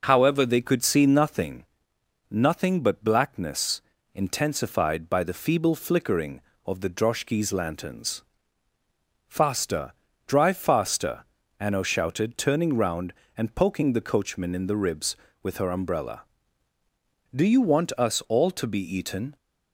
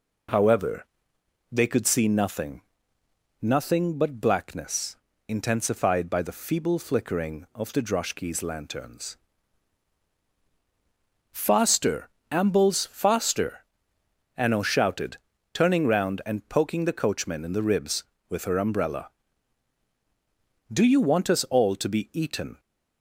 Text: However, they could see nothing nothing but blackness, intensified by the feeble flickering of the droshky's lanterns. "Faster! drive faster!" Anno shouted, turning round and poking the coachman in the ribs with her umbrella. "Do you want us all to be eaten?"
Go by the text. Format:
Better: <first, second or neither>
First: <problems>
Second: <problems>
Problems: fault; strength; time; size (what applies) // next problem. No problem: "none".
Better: first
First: pauses between "nothing" and "nothing"; noticeable; at 1.6 s; 0.66 s long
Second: pauses between "nothing" and "nothing"; noticeable; at 2.6 s; 0.80 s long // says "ambles" for "drive"; at 12.2 s